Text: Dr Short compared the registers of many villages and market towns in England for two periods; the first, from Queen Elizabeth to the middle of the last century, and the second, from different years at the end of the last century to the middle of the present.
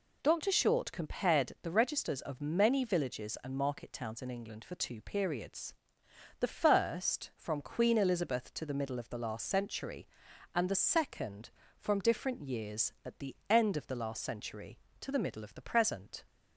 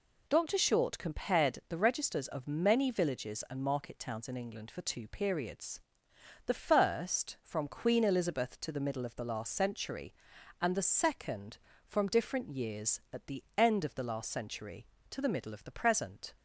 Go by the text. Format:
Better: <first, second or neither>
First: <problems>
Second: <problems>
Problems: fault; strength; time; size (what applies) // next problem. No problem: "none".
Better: neither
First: none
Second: none